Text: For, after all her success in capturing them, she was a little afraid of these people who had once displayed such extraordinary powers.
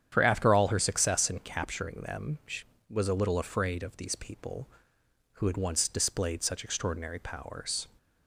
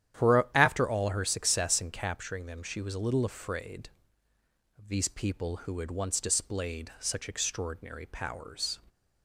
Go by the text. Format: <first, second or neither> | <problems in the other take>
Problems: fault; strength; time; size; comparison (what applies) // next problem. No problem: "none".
neither | starts louder than the rest; strong; the same in both